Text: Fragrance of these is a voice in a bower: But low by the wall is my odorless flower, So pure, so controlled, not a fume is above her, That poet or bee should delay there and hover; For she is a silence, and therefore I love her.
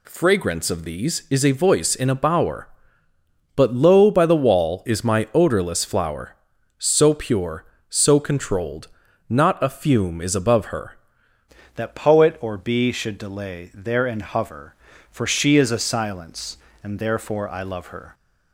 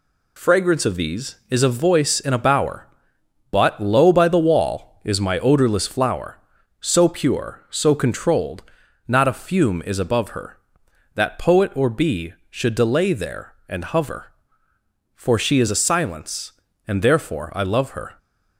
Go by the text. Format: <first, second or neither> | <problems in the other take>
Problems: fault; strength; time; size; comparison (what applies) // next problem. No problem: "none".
second | changes voice at "That"; from 11.7 s on; 6.4 s long